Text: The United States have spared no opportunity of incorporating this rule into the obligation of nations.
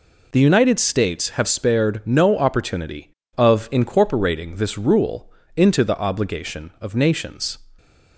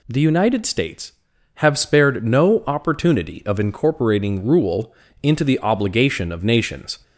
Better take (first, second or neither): first